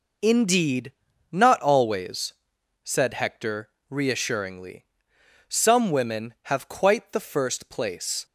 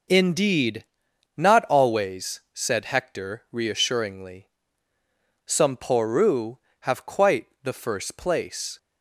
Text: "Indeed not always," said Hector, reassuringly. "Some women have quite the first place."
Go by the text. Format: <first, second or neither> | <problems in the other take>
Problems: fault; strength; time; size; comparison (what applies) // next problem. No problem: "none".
first | pauses between "Indeed" and "not"; noticeable; at 0.8 s; 0.50 s long; also in the first // says "poru" for "women"; at 5.7 s // pauses between "quite" and "the"; slight; at 7.4 s; 0.16 s long